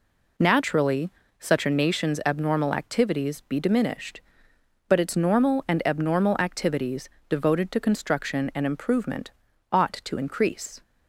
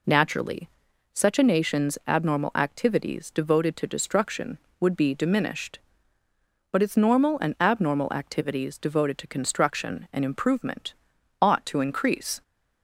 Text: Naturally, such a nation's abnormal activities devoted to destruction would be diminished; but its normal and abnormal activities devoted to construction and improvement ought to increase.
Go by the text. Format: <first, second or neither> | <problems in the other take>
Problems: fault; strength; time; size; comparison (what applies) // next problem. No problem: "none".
second | skips "devoted to destruction would"; at 3.4 s // pauses between "activities" and "devoted"; slight; at 7.0 s; 0.20 s long // pauses between "improvement" and "ought"; at 9.3 s; 0.40 s long; noticeable in the second